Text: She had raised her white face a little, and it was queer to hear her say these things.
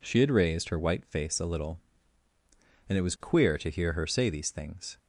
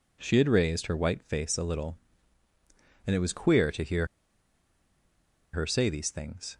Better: first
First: none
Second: pauses between "hear" and "her"; strong; at 4.0 s; 1.4 s long

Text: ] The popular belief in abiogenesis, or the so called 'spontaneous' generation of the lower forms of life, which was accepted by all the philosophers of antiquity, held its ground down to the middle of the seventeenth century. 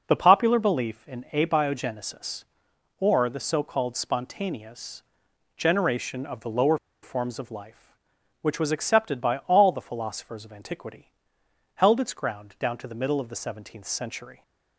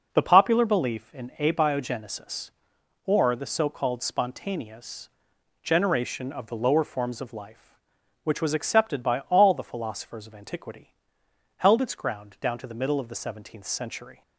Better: second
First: pauses between "spontaneous" and "generation"; noticeable; at 5.0 s; 0.54 s long // pauses between "lower" and "forms"; slight; at 6.7 s; 0.26 s long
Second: pauses between "spontaneous" and "generation"; noticeable; at 5.0 s; 0.54 s long

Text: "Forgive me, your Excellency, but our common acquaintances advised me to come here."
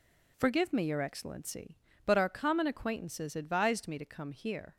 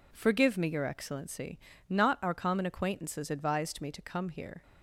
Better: first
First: none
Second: says "not" for "but"; at 1.8 s

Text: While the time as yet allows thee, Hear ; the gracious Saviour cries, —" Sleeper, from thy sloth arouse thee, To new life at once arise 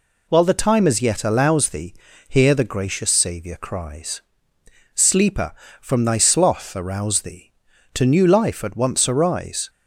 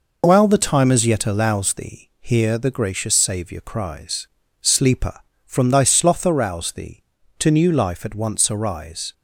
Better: neither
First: none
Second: none

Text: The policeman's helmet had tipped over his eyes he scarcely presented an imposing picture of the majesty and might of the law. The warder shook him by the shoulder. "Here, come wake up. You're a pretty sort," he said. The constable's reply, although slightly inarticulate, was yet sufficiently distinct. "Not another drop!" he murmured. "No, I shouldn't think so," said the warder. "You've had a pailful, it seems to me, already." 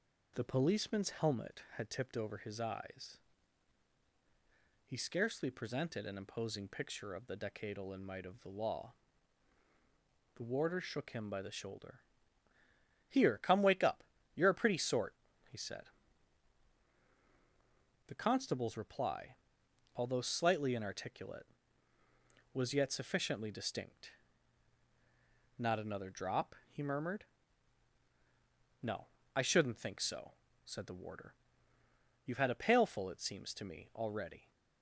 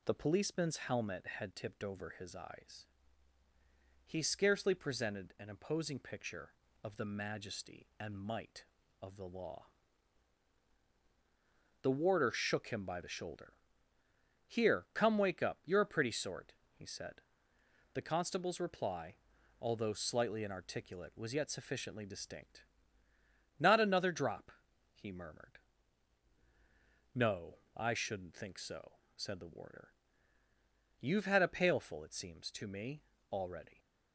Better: second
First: pauses between "eyes" and "he"; strong; at 3.1 s; 1.6 s long // says "decadal" for "majesty"; at 7.3 s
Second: pauses between "eyes" and "he"; at 2.8 s; 1.2 s long

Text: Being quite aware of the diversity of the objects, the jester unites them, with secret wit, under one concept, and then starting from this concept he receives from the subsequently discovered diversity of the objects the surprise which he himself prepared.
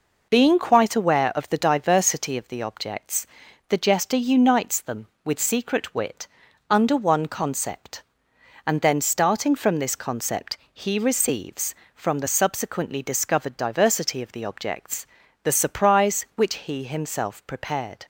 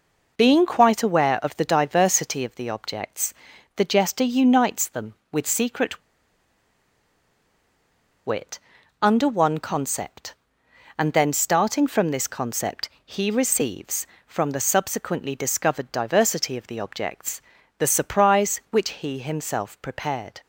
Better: first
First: pauses between "concept" and "he"; slight; at 10.5 s; 0.16 s long // pauses between "objects" and "the"; at 15.0 s; 0.38 s long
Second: pauses between "secret" and "wit"; strong; at 6.0 s; 2.2 s long // pauses between "concept" and "he"; slight; at 12.8 s; 0.16 s long // pauses between "objects" and "the"; at 17.3 s; 0.38 s long

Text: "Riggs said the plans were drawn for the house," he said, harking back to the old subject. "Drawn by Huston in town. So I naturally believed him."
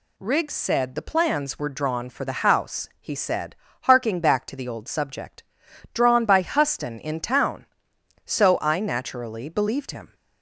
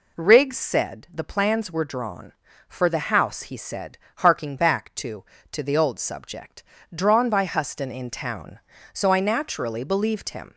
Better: first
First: none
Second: says "to" twice; at 5.5 s

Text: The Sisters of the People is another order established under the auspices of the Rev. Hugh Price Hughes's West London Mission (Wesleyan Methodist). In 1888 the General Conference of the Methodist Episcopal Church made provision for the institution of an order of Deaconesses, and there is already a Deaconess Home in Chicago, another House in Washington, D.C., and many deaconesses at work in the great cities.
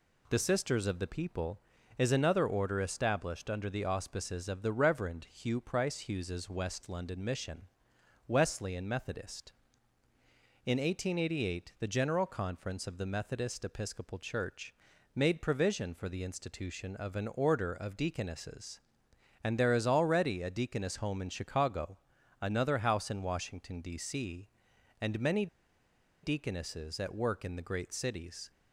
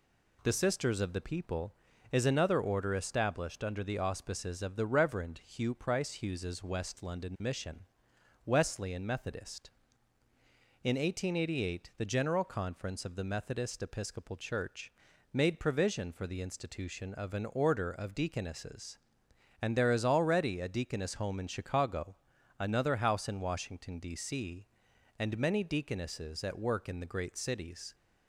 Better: second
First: pauses between "Church" and "made"; at 14.7 s; 0.40 s long // pauses between "many" and "deaconesses"; noticeable; at 25.4 s; 0.76 s long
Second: pauses between "Church" and "made"; at 14.9 s; 0.40 s long

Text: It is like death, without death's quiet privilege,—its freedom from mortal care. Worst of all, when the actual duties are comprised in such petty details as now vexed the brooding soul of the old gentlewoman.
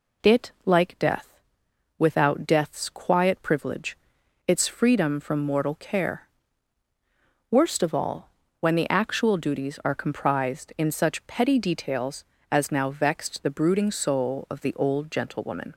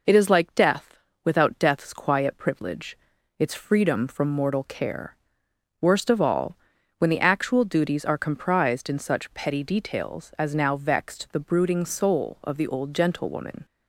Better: second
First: skips "is"; at 0.5 s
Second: none

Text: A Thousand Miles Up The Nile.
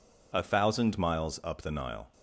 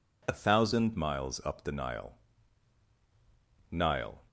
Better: first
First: none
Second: says "Nile" twice; at 3.7 s

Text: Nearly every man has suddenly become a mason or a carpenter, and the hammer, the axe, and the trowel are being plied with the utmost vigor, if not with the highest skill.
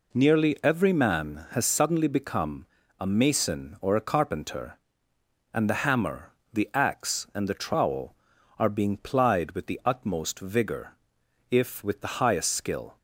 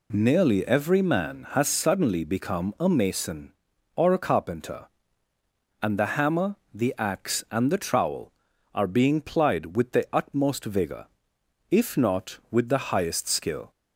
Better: second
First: pauses between "become" and "a"; slight; at 2.6 s; 0.34 s long // skips "not"; at 11.8 s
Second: none

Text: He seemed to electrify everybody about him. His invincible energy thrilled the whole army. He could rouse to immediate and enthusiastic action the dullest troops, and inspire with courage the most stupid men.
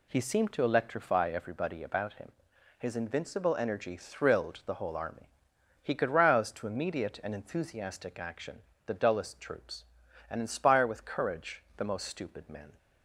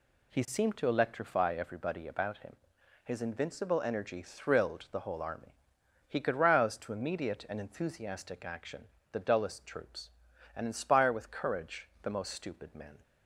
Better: neither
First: pauses between "action" and "the"; slight; at 8.6 s; 0.26 s long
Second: pauses between "action" and "the"; slight; at 8.8 s; 0.26 s long

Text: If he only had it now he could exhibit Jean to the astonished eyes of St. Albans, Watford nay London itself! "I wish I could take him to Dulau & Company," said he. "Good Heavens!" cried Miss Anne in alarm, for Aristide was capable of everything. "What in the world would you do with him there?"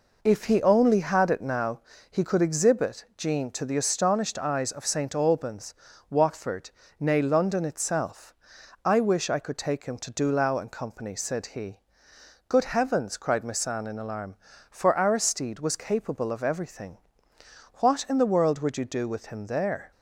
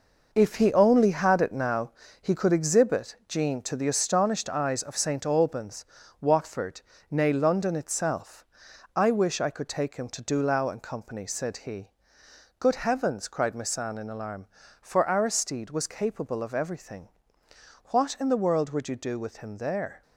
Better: first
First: pauses between "now" and "he"; slight; at 1.8 s; 0.30 s long // pauses between "Watford" and "nay"; slight; at 6.6 s; 0.30 s long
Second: gets quieter; strong; throughout; 8.5 dB // pauses between "now" and "he"; slight; at 1.9 s; 0.30 s long // pauses between "Watford" and "nay"; slight; at 6.7 s; 0.30 s long

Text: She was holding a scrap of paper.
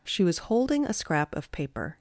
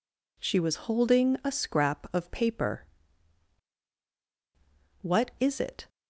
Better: first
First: none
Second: goes on to say "What is it"; noticeable; from 5.0 s on; 0.86 s long

